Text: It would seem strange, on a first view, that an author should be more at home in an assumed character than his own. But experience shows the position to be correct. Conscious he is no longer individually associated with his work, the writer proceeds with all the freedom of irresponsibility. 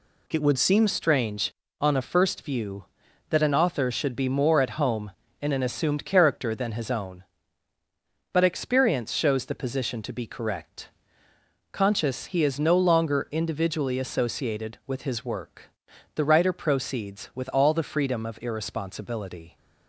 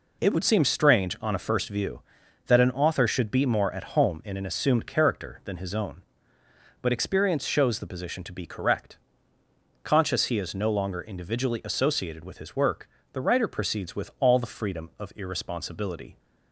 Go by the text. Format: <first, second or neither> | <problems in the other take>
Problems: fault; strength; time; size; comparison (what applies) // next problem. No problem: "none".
second | changes voice at "strange"; from 0.8 s on; 18.7 s long